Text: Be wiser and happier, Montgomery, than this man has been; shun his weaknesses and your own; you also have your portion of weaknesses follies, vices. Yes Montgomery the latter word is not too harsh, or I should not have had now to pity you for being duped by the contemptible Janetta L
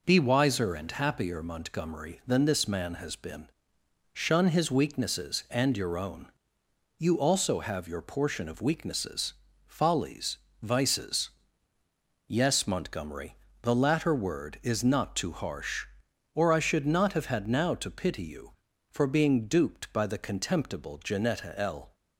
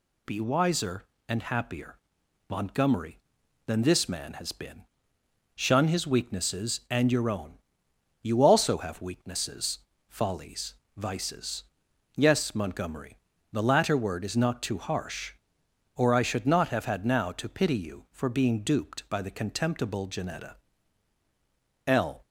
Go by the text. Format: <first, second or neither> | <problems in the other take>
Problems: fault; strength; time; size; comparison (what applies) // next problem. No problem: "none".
first | skips "your portion of"; at 9.0 s // pauses between "weaknesses" and "follies"; slight; at 9.8 s; 0.28 s long; slight in the first // pauses between "Montgomery" and "the"; slight; at 13.1 s; 0.34 s long; slight in the first // pauses between "Janetta" and "L"; strong; at 20.5 s; 1.3 s long